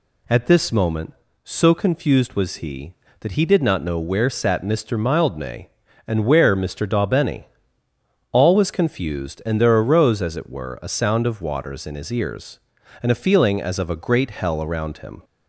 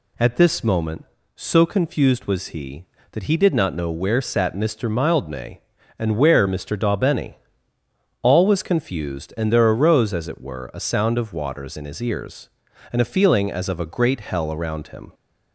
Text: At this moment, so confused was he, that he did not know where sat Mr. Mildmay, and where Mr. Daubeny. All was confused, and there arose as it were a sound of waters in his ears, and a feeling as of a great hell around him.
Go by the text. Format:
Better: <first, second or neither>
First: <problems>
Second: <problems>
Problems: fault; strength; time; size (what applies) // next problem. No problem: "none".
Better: neither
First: none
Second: none